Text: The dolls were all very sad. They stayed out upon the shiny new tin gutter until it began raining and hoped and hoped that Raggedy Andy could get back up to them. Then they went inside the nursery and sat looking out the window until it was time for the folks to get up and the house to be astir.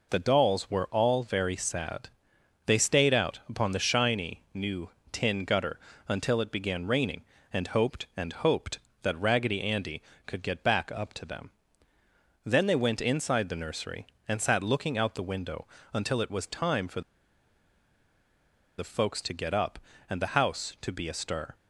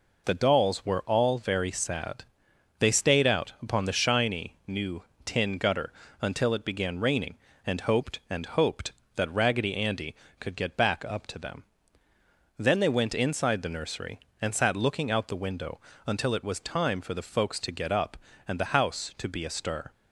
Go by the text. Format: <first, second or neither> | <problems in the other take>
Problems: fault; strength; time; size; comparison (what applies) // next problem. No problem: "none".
second | pauses between "new" and "tin"; slight; at 4.8 s; 0.22 s long; slight in the second // pauses between "gutter" and "until"; slight; at 5.7 s; 0.28 s long; slight in the second // pauses between "window" and "until"; slight; at 15.6 s; 0.26 s long; slight in the second // pauses between "for" and "the"; strong; at 17.0 s; 1.7 s long